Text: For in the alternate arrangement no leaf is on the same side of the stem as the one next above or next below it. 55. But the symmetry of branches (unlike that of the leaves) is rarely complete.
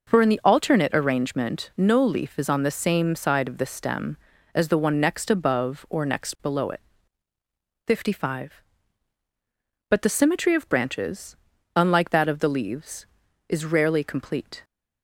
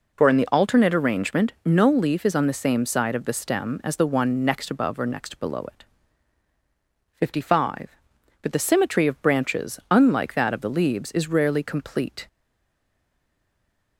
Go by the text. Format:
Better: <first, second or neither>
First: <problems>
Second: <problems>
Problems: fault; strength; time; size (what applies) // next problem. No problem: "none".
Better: first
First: none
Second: stays silent after the last word; noticeable; from 12.2 s on; 1.7 s long